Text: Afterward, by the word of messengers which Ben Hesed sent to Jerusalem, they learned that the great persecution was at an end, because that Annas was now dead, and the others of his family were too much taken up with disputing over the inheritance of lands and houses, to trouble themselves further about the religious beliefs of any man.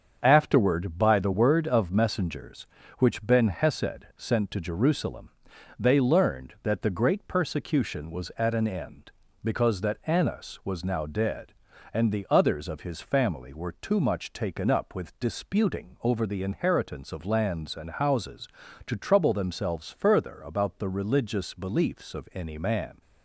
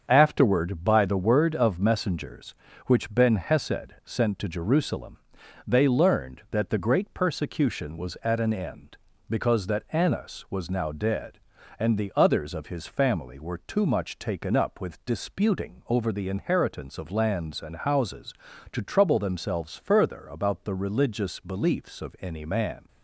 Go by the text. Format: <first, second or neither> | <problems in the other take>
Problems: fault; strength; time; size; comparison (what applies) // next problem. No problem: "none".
neither | starts louder than the rest; the same in both